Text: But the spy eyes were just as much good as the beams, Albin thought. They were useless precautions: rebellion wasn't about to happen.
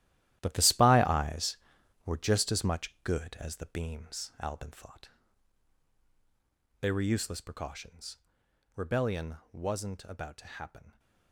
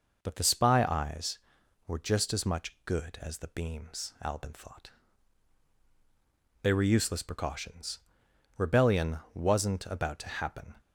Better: second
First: gets quieter; strong; throughout; 12 dB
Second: none

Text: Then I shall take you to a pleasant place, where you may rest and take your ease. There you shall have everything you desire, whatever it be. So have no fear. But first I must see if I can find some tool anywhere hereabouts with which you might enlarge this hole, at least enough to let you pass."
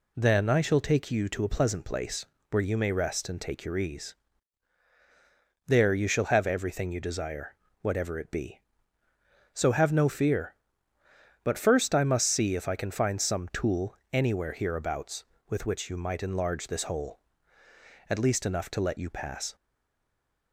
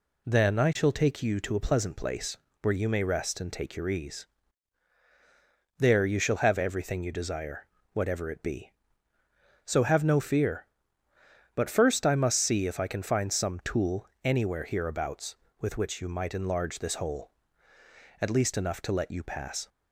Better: second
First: pauses between "tool" and "anywhere"; slight; at 13.9 s; 0.16 s long // stays silent after the last word; from 19.5 s on; 1.0 s long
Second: pauses between "tool" and "anywhere"; slight; at 14.0 s; 0.16 s long

